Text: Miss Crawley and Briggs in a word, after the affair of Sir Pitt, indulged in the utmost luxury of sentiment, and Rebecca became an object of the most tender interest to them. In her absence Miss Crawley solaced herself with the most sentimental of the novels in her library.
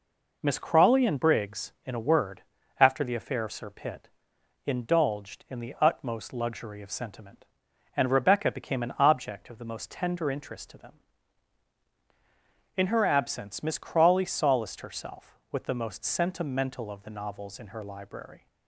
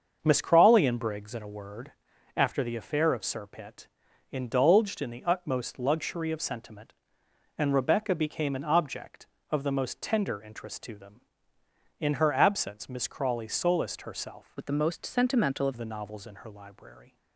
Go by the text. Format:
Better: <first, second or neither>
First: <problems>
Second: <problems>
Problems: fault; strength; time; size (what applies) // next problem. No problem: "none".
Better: first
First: none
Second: starts louder than the rest; until 1.2 s; 6.5 dB // changes voice from "with" to "of"; from 14.5 to 15.7 s; 1.2 s long